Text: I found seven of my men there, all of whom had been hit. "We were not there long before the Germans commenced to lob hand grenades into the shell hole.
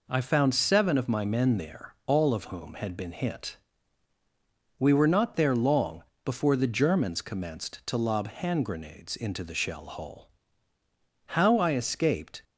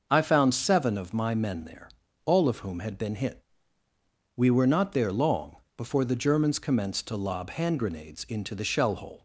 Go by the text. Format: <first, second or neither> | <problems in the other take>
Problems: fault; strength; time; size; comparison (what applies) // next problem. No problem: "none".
second | pauses between "long" and "before"; slight; at 6.0 s; 0.20 s long; slight in the second // goes on to say "How I escaped"; noticeable; from 11.2 s on; 1.1 s long